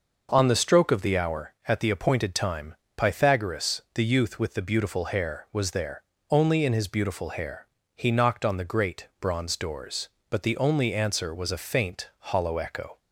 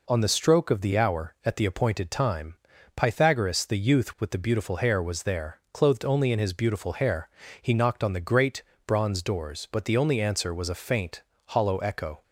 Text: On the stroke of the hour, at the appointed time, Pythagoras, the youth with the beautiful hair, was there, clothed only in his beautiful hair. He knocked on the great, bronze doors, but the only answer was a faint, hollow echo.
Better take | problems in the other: second | skips "clothed"; at 6.1 s

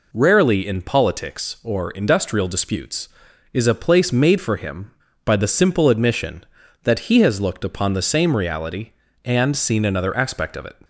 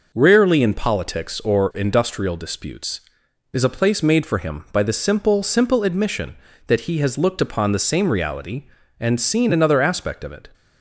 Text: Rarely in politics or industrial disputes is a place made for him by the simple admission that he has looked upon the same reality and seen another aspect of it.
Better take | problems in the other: first | says "simple" twice; at 5.4 s

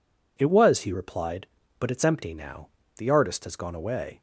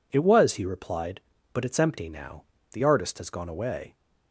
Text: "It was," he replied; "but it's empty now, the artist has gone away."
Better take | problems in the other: neither | none

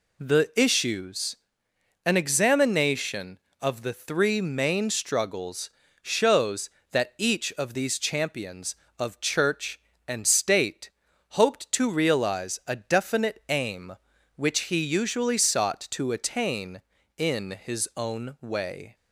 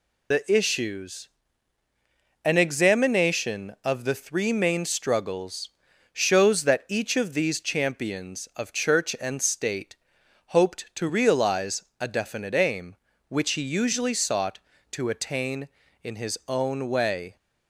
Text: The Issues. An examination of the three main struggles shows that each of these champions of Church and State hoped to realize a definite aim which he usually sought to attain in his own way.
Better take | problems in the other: first | loses the start of "The"; at 0.3 s; 105 ms // pauses between "struggles" and "shows"; at 5.6 s; 0.44 s long; slight in the first // pauses between "State" and "hoped"; noticeable; at 9.9 s; 0.52 s long; also in the first // pauses between "realize" and "a"; slight; at 11.8 s; 0.18 s long

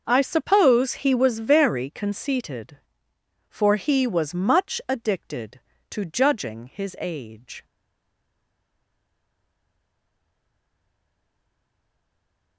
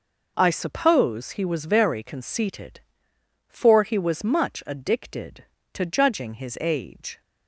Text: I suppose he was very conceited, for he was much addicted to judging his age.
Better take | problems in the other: second | starts louder than the rest; noticeable; until 1.0 s; 6 dB // stays silent after the last word; strong; from 7.6 s on; 4.9 s long

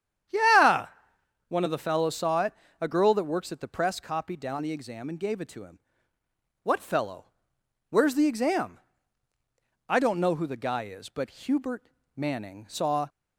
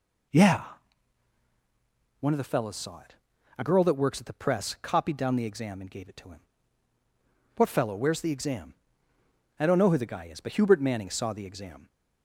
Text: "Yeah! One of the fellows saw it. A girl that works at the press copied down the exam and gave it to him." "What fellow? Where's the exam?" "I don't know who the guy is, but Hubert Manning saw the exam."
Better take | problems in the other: second | starts louder than the rest; strong; until 1.9 s; 9 dB // pauses between "Hubert" and "Manning"; slight; at 11.8 s; 0.32 s long // stops before "the exam"; at 13.0 s

